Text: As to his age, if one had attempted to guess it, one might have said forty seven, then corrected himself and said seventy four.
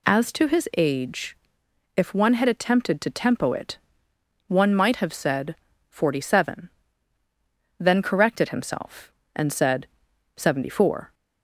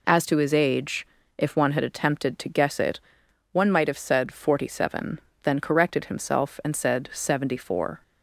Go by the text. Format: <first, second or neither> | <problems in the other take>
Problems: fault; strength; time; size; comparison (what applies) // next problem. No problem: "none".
second | says "tempo" for "guess"; at 3.0 s // pauses between "said" and "forty"; slight; at 5.5 s; 0.32 s long // pauses between "said" and "seventy"; noticeable; at 9.8 s; 0.50 s long